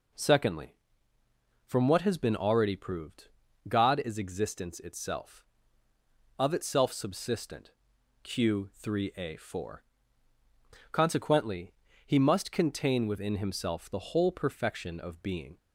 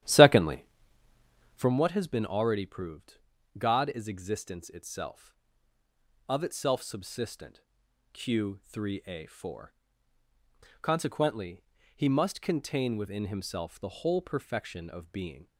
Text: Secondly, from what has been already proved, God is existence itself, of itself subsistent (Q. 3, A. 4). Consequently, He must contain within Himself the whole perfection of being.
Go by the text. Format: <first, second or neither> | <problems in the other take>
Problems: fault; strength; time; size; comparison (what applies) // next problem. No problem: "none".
first | starts louder than the rest; strong; until 1.7 s; 12 dB